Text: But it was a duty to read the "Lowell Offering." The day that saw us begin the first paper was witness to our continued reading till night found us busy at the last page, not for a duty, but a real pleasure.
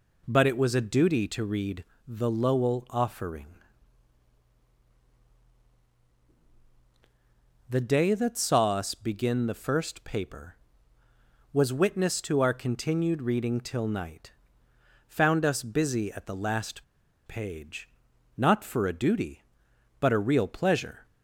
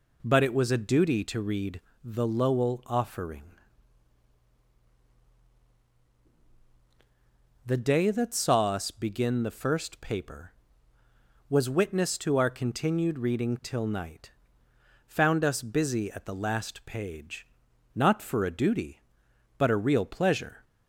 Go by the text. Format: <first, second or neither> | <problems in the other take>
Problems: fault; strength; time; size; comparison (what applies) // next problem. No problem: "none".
second | pauses between "read" and "the"; slight; at 1.8 s; 0.22 s long; slight in the second // pauses between "night" and "found"; noticeable; at 14.3 s; 0.76 s long; noticeable in the second // pauses between "last" and "page"; at 16.8 s; 0.43 s long